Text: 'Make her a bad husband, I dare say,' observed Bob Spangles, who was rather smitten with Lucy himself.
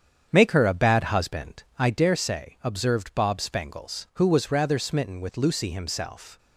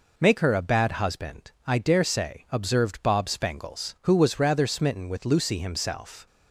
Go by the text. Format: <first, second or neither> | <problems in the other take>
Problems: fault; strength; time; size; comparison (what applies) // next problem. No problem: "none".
second | starts louder than the rest; strong; until 2.2 s; 8 dB